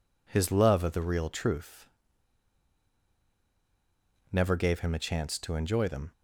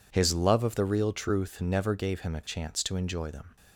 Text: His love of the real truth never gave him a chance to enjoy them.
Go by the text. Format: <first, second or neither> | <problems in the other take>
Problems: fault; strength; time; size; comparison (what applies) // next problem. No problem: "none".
second | pauses between "truth" and "never"; strong; at 1.8 s; 2.4 s long